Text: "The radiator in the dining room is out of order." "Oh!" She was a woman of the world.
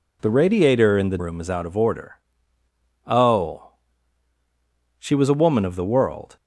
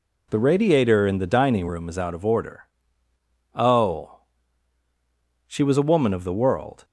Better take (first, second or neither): second